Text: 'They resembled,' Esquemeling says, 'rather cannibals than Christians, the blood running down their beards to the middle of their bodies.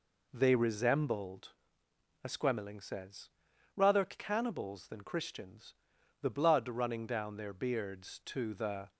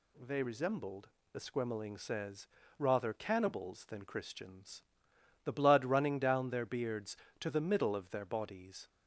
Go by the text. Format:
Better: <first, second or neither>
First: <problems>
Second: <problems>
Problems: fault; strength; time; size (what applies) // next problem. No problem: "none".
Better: second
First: stops before "middle of their bodies"; at 8.9 s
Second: none